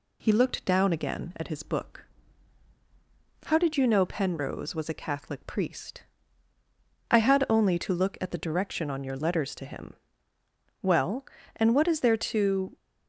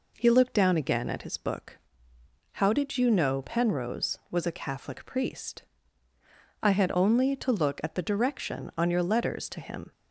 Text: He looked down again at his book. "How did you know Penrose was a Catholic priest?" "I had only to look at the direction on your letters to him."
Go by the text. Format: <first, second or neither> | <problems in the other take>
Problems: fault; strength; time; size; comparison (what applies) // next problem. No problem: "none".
second | goes on to say "Well and what is there to"; strong; from 10.8 s on; 1.9 s long